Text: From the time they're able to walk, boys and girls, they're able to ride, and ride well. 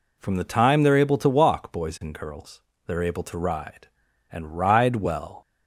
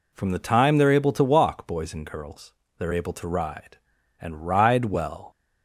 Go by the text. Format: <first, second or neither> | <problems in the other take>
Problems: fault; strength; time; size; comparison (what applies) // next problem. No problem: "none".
neither | none